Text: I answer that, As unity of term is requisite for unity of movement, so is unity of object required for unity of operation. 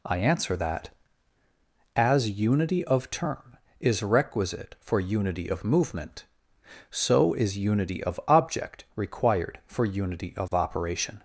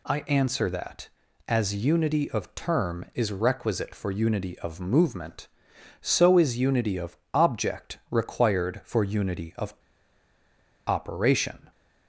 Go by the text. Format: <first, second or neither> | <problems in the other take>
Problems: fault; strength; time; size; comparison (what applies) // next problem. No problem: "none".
first | pauses between "of" and "object"; slight; at 7.1 s; 0.18 s long // pauses between "of" and "operation"; at 9.7 s; 1.1 s long